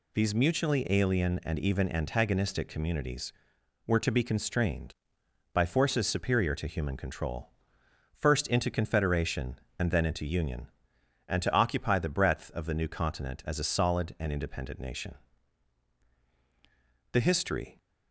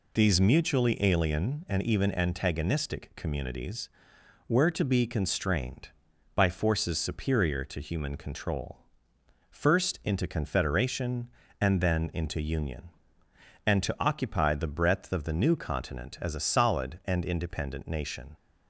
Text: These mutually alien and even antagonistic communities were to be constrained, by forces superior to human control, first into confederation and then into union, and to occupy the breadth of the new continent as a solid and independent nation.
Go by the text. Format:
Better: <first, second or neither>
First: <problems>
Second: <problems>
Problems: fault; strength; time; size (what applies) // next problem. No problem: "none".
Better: second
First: goes on to say "The history"; noticeable; from 17.1 s on; 0.66 s long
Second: none